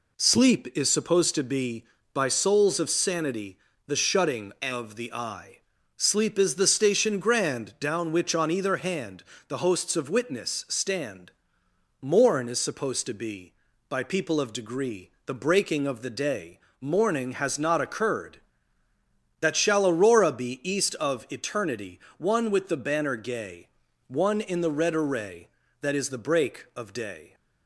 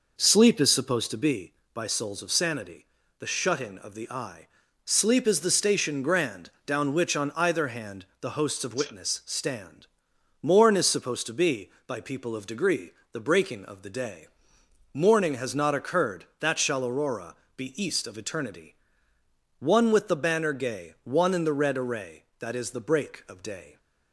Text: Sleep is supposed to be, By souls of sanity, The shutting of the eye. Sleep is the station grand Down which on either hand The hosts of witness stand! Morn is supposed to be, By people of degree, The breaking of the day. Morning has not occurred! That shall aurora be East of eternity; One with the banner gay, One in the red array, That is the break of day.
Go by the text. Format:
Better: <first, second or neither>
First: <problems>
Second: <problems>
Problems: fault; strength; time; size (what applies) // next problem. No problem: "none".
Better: first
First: pauses between "hand" and "The"; slight; at 9.2 s; 0.24 s long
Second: starts louder than the rest; noticeable; until 1.4 s; 5 dB // pauses between "grand" and "Down"; slight; at 6.4 s; 0.16 s long // pauses between "hand" and "The"; slight; at 8.0 s; 0.16 s long // pauses between "aurora" and "be"; slight; at 17.3 s; 0.20 s long